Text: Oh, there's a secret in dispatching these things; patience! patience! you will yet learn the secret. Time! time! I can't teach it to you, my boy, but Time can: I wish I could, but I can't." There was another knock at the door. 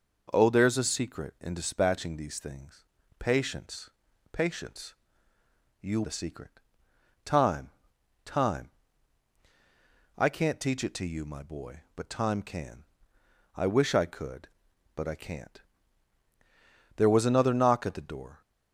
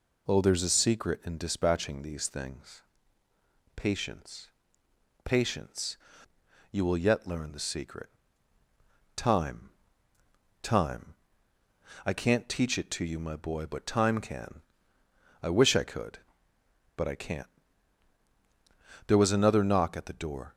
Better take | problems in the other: second | skips "will yet learn"; at 6.0 s

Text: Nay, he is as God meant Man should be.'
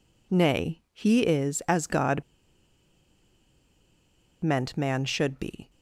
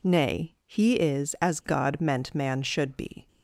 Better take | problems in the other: second | pauses between "God" and "meant"; strong; at 2.2 s; 2.2 s long

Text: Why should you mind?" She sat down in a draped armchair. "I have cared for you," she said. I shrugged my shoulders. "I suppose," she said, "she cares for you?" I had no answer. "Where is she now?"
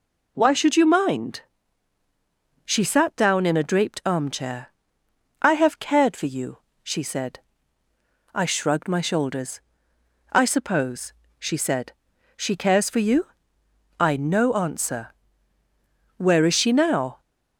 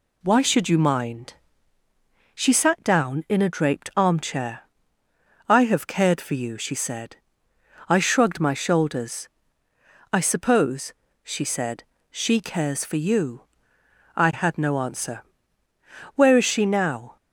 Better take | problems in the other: second | skips "had"; at 14.1 s

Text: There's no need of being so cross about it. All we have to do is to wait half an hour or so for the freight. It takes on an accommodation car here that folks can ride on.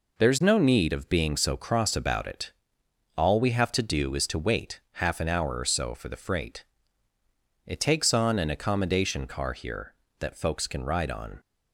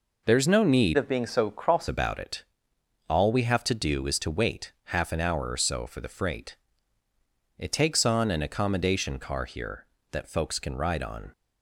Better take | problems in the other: first | changes voice from "of" to "cross"; from 0.9 to 1.8 s; 0.9 s long

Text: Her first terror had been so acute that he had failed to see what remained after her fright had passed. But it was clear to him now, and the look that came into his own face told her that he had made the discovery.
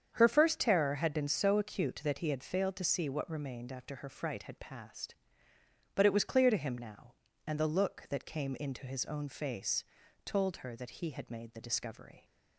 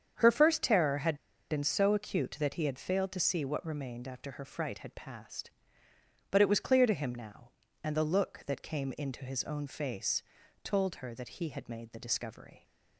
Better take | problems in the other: first | starts louder than the rest; strong; until 1.5 s; 8 dB; strong in the first // pauses between "had" and "been"; slight; at 1.1 s; 0.34 s long // pauses between "face" and "told"; at 10.2 s; 0.40 s long; also in the first

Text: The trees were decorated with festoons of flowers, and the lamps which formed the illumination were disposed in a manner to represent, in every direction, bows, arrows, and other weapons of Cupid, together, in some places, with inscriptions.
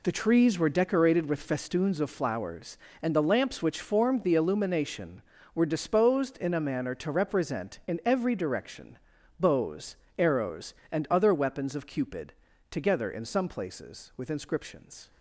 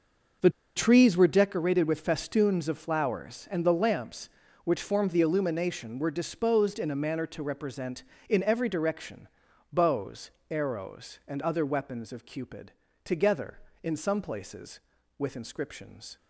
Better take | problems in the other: first | starts louder than the rest; noticeable; until 1.6 s; 6 dB // pauses between "The" and "trees"; slight; at 0.4 s; 0.26 s long

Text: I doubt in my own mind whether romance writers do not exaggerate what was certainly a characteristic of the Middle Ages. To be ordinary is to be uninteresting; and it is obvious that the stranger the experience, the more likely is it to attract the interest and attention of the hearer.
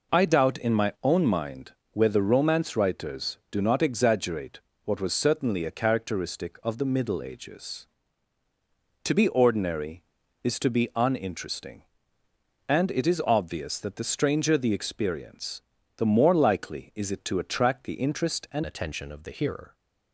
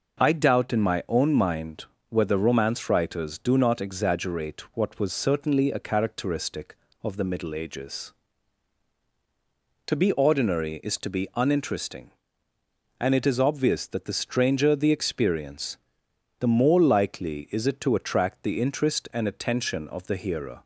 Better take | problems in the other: second | pauses between "mind" and "whether"; slight; at 1.7 s; 0.22 s long; slight in the second // pauses between "exaggerate" and "what"; slight; at 4.5 s; 0.26 s long // changes voice at "attention"; from 18.6 s on; 1.1 s long

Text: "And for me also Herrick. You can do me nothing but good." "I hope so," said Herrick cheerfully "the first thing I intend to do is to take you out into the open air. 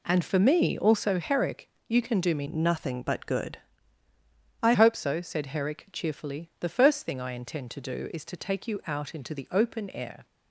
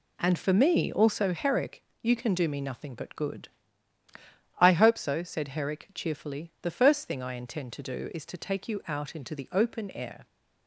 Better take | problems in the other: second | changes voice from "nothing" to "I"; from 2.4 to 4.7 s; 2.3 s long

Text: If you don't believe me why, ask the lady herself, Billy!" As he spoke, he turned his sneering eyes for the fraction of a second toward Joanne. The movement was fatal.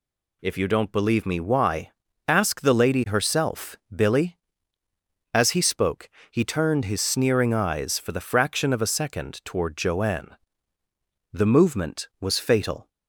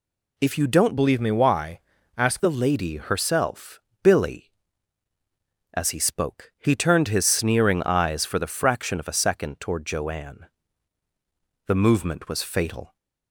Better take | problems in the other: first | changes voice from "believe" to "ask"; from 0.9 to 2.4 s; 1.5 s long

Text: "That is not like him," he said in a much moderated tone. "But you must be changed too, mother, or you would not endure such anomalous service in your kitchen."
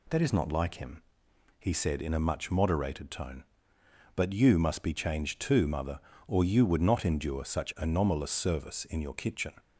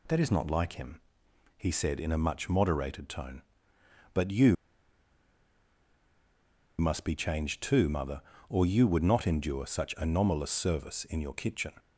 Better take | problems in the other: first | pauses between "you" and "must"; strong; at 4.5 s; 2.2 s long

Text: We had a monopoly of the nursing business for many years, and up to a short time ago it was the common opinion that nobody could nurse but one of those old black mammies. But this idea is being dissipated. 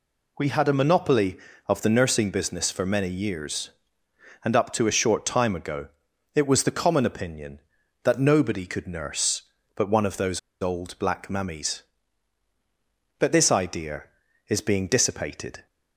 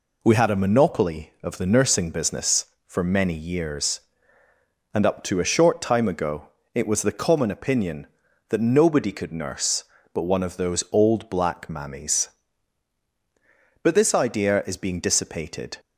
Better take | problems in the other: second | pauses between "ago" and "it"; noticeable; at 5.8 s; 0.48 s long; slight in the second // pauses between "those" and "old"; slight; at 10.3 s; 0.22 s long

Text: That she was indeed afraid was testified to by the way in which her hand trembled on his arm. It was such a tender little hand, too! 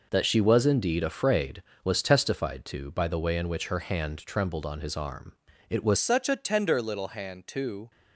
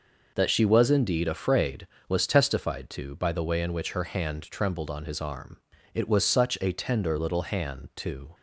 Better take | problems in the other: second | changes voice at "such"; from 5.9 s on; 2.0 s long

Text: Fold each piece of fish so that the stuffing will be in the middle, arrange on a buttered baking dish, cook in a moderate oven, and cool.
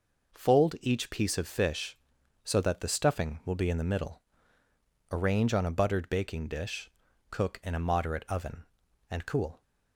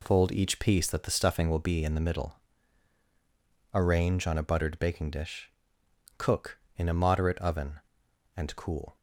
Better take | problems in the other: first | skips "of fish so"; at 0.8 s

